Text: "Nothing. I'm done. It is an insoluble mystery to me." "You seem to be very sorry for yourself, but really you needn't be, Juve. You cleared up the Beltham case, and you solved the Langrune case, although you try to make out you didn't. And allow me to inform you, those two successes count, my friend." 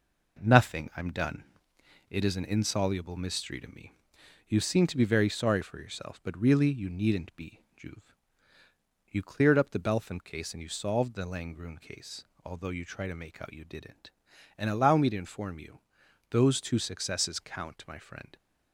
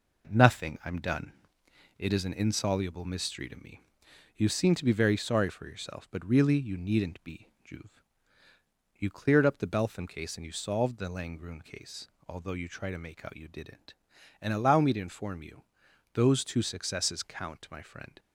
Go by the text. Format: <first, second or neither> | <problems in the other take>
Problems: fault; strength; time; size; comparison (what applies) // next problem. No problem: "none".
neither | none